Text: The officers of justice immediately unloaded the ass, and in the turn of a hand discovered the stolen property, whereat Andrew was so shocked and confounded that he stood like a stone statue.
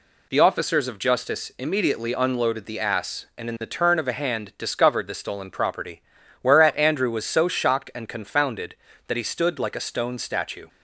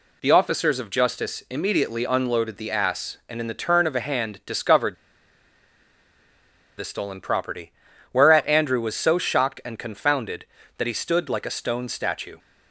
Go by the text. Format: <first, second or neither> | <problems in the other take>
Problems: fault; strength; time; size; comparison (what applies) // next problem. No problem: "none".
first | pauses between "discovered" and "the"; strong; at 4.9 s; 1.8 s long